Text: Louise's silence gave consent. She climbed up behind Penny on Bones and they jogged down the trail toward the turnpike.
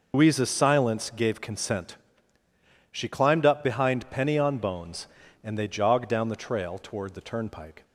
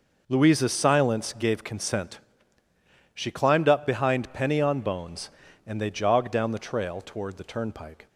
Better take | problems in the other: second | loses the start of "Louise's"; at 0.1 s; 100 ms

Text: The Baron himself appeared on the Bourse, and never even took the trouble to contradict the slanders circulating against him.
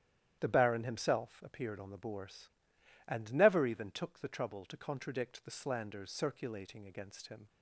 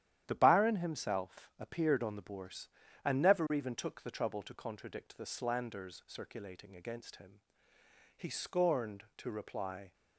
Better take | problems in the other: first | starts louder than the rest; strong; until 1.2 s; 11 dB; strong in the first // goes on to say "He scorned to reply"; strong; from 8.1 s on; 1.7 s long

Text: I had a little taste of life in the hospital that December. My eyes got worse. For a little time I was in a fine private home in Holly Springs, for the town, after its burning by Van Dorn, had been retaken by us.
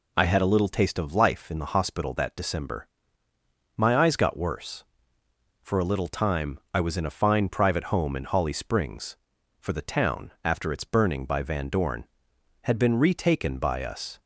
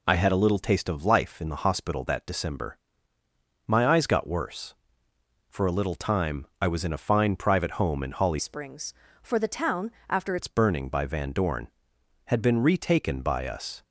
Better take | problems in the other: first | pauses between "time" and "I"; slight; at 6.4 s; 0.16 s long; slight in the first // changes voice from "Springs" to "after"; from 8.3 to 10.3 s; 2.0 s long

